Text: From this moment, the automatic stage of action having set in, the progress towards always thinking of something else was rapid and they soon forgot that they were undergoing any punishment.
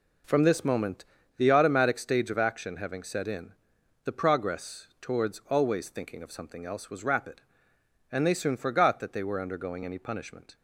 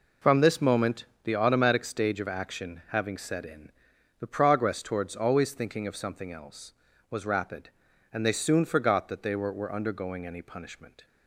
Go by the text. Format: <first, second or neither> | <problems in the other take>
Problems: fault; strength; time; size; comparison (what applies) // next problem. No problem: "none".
first | says "were" twice; at 9.5 s